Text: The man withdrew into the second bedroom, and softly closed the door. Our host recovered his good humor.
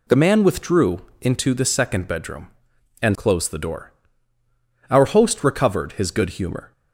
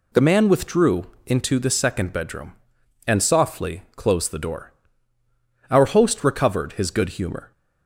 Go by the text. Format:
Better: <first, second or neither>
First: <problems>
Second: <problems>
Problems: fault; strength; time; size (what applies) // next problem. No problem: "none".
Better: second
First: pauses between "withdrew" and "into"; slight; at 1.0 s; 0.20 s long // skips "softly"; at 3.1 s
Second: pauses between "withdrew" and "into"; slight; at 1.0 s; 0.20 s long